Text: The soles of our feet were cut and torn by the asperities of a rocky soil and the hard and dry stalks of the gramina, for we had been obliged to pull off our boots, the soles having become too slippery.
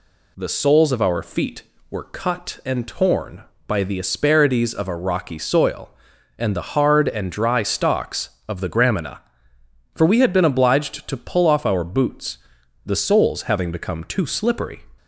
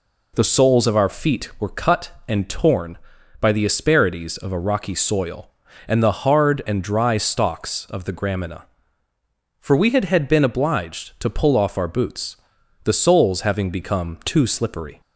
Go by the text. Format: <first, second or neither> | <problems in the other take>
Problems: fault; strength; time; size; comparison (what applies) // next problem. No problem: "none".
first | says "had" twice; at 10.0 s